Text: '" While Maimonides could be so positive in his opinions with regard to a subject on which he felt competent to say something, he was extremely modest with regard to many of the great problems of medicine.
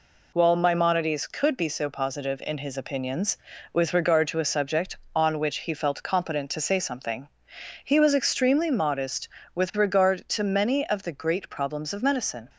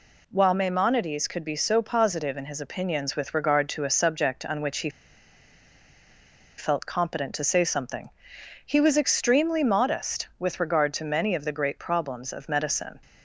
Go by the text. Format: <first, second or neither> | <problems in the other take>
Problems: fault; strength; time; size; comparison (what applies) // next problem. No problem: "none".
first | pauses between "he" and "felt"; strong; at 4.8 s; 1.6 s long